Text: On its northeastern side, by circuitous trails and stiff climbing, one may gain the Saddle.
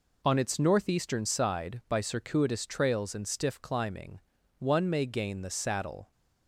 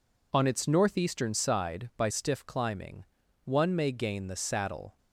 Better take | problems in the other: first | skips "circuitous trails and"; at 2.0 s

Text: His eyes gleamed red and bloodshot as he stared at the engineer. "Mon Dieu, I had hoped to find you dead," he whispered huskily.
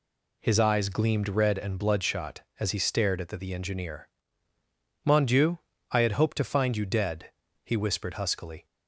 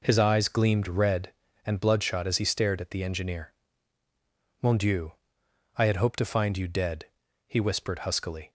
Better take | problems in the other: second | says "the" twice; at 3.3 s

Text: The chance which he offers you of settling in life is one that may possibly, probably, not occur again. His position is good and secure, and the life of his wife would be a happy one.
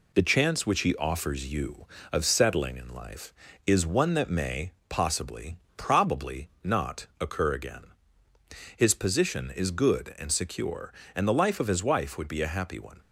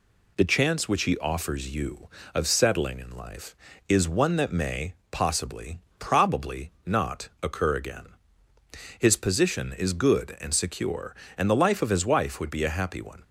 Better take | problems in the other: second | gets quieter; slight; throughout; 3 dB // pauses between "may" and "possibly"; slight; at 4.7 s; 0.16 s long; slight in the second

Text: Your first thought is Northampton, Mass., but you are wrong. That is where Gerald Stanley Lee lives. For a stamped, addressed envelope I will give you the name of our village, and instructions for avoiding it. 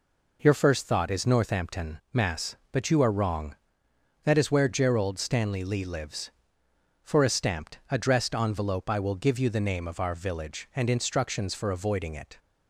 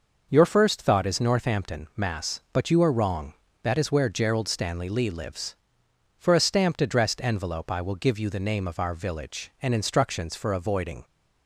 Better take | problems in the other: first | stops before "it"; at 11.0 s

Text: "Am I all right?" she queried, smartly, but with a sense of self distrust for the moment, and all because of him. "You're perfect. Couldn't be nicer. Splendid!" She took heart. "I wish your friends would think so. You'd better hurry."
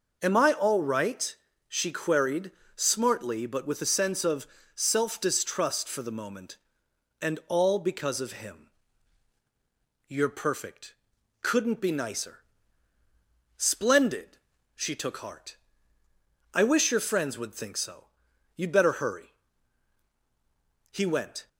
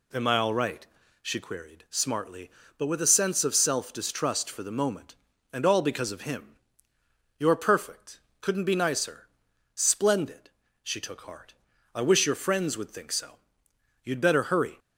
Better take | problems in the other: second | pauses between "of" and "self"; slight; at 4.4 s; 0.26 s long // goes on to say "He went"; from 20.8 s on; 0.58 s long

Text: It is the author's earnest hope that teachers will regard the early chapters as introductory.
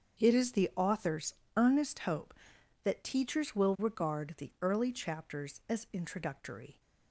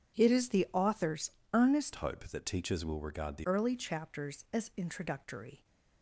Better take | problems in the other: first | starts louder than the rest; strong; until 1.2 s; 7 dB; also in the first // pauses between "author's" and "earnest"; slight; at 1.3 s; 0.20 s long; slight in the first // changes voice from "hope" to "the"; from 1.9 to 3.4 s; 1.5 s long

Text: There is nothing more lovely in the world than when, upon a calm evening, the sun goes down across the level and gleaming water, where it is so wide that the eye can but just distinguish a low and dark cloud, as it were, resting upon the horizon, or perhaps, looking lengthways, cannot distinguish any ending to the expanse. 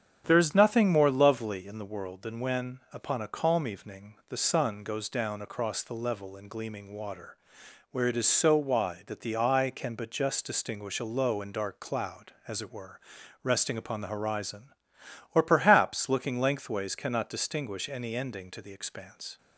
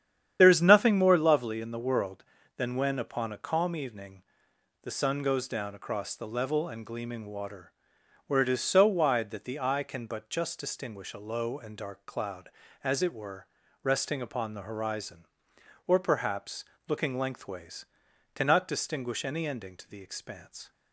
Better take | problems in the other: first | loses the start of "There"; at 0.3 s; 35 ms // starts louder than the rest; strong; until 1.4 s; 9.5 dB; strong in the first

